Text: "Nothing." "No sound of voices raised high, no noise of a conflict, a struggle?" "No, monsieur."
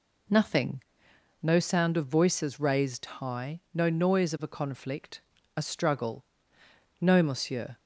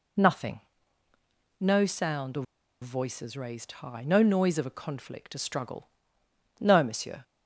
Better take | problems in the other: first | pauses between "of" and "voices"; at 2.4 s; 0.37 s long

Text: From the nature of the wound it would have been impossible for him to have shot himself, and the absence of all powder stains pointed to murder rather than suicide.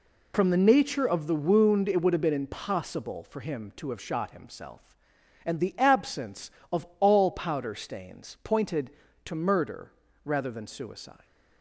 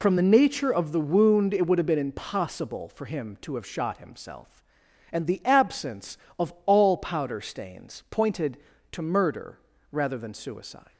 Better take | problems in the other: neither | pauses between "murder" and "rather"; slight; the same in both

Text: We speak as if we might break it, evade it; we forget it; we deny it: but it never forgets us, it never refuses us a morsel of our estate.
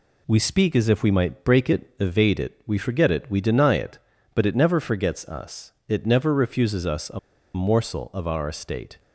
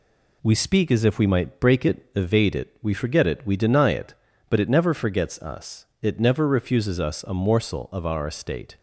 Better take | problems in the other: second | pauses between "a" and "morsel"; slight; at 7.1 s; 0.35 s long

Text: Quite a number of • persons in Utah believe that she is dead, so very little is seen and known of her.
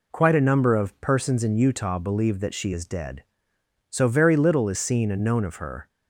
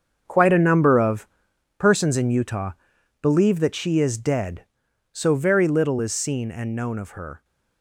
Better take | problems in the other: first | gets quieter; strong; throughout; 12 dB // pauses between "Utah" and "believe"; noticeable; at 2.7 s; 0.50 s long

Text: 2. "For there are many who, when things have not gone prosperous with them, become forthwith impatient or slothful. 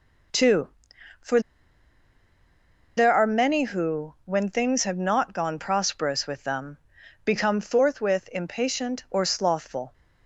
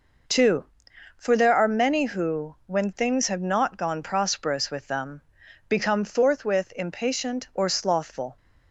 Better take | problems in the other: second | pauses between "For" and "there"; strong; at 1.3 s; 1.5 s long

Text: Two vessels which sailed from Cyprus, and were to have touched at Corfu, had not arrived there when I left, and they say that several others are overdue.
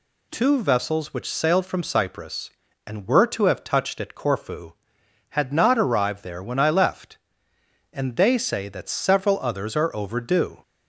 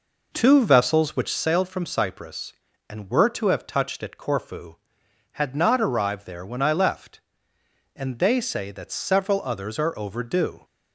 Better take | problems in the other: first | starts louder than the rest; noticeable; until 1.5 s; 4.5 dB

